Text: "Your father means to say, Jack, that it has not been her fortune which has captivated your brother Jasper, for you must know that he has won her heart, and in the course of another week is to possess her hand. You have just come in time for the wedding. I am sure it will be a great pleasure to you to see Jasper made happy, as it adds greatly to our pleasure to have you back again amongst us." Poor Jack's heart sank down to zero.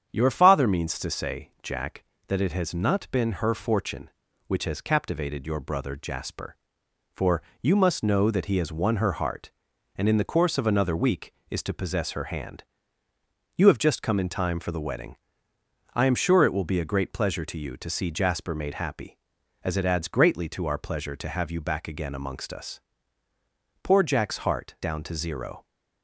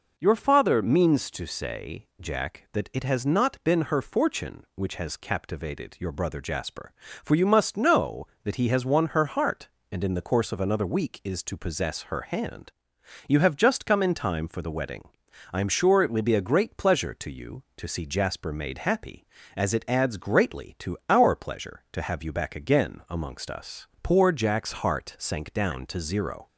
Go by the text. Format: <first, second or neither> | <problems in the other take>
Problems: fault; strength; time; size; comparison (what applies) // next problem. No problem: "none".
second | starts louder than the rest; strong; until 1.1 s; 8.5 dB // pauses between "for" and "you"; slight; at 7.4 s; 0.18 s long // skips "sank"; at 24.7 s